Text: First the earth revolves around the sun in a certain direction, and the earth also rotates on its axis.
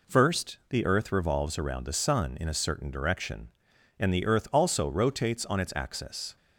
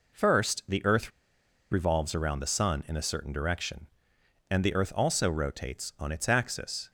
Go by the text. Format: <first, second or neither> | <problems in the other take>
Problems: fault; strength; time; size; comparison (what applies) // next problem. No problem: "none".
first | pauses between "earth" and "revolves"; noticeable; at 1.0 s; 0.61 s long